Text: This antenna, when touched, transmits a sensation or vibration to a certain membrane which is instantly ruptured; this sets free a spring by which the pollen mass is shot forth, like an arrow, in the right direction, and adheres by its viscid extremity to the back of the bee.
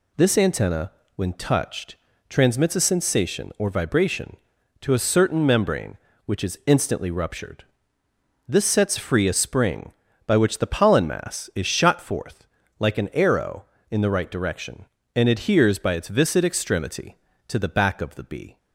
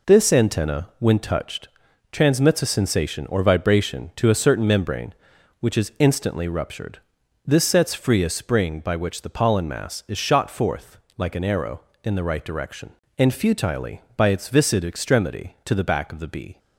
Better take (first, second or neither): first